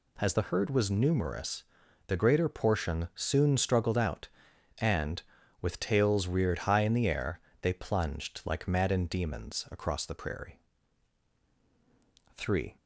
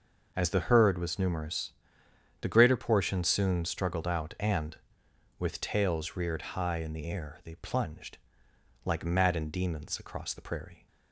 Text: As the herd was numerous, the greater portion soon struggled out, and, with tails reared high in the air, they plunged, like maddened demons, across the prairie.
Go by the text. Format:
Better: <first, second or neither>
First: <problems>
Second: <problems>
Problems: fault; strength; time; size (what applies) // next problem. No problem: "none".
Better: second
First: goes on to say "Three"; slight; from 12.3 s on; 0.38 s long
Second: none